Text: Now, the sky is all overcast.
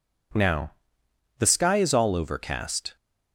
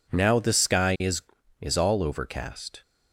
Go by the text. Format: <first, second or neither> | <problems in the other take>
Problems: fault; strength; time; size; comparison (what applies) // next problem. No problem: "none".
first | says "is" twice; at 1.6 s